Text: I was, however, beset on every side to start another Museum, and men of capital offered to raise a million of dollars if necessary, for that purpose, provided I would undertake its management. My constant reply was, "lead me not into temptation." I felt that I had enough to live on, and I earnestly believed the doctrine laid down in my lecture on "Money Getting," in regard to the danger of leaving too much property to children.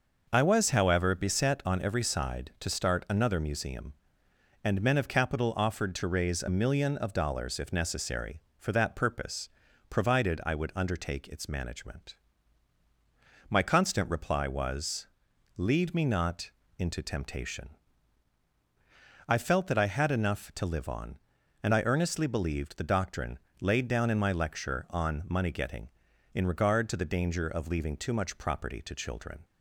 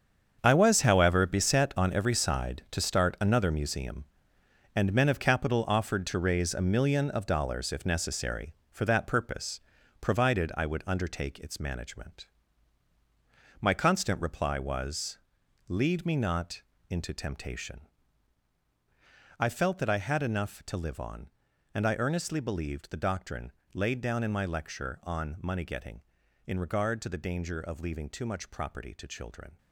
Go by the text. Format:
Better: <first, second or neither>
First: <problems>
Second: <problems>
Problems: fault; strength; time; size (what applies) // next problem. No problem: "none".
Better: first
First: pauses between "not" and "into"; slight; at 16.5 s; 0.26 s long // pauses between "doctrine" and "laid"; slight; at 23.3 s; 0.24 s long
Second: gets quieter; strong; throughout; 11.5 dB // pauses between "not" and "into"; slight; at 16.6 s; 0.26 s long // pauses between "doctrine" and "laid"; slight; at 23.4 s; 0.24 s long